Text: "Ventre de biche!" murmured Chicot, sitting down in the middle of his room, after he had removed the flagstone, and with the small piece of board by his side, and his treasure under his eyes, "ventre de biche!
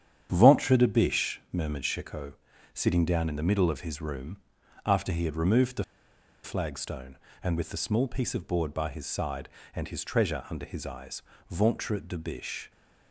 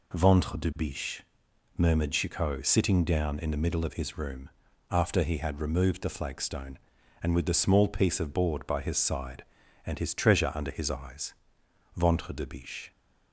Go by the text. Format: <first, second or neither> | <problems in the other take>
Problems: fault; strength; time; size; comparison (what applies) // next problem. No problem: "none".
second | starts louder than the rest; strong; until 1.3 s; 9 dB // pauses between "the" and "flagstone"; noticeable; at 5.8 s; 0.61 s long